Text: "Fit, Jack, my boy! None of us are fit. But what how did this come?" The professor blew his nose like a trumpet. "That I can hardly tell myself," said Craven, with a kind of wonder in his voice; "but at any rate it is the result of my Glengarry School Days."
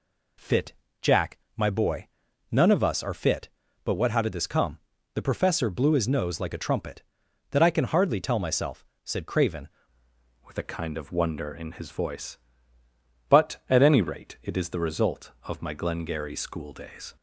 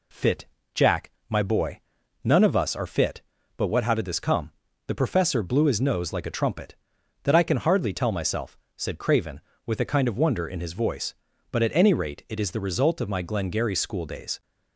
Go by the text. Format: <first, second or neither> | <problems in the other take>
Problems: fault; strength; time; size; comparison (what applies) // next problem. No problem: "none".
second | changes voice at "with"; from 10.4 s on; 6.7 s long